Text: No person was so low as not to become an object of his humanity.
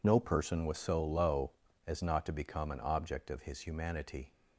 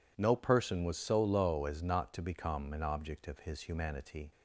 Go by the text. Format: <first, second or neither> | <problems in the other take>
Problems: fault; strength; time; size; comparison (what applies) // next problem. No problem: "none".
neither | none